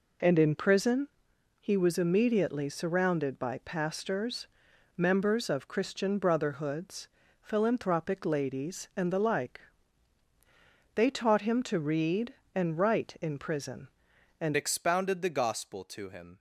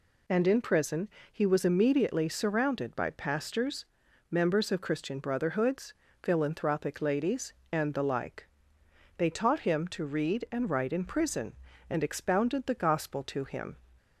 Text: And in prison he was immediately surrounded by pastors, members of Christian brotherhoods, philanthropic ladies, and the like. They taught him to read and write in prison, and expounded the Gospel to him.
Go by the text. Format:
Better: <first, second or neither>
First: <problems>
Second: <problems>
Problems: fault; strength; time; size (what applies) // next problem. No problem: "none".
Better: second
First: pauses between "prison" and "he"; noticeable; at 1.0 s; 0.52 s long // changes voice at "expounded"; from 14.5 s on; 1.8 s long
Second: pauses between "prison" and "he"; slight; at 1.0 s; 0.24 s long